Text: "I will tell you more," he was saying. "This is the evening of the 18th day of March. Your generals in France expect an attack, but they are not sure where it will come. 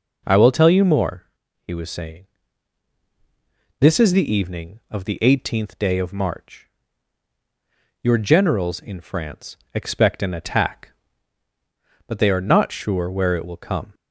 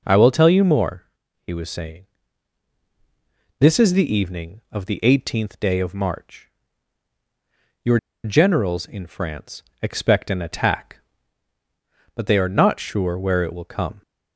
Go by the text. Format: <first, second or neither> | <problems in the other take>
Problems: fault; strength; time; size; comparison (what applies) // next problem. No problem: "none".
first | pauses between "Your" and "generals"; slight; at 7.9 s; 0.25 s long // pauses between "France" and "expect"; slight; at 9.6 s; 0.22 s long; slight in the first